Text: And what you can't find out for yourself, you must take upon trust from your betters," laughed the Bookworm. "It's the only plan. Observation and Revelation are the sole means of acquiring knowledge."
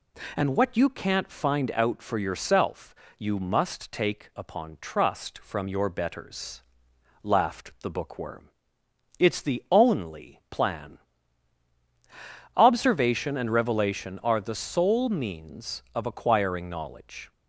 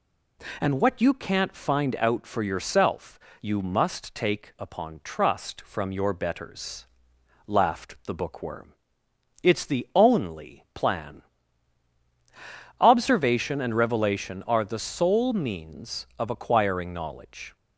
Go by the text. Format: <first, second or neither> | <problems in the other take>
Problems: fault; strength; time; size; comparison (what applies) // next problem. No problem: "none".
neither | none